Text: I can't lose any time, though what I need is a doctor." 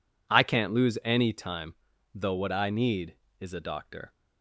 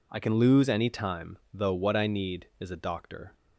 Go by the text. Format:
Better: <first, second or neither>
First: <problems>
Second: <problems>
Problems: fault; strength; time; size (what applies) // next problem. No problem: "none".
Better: first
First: none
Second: says "can" for "can't"; at 0.1 s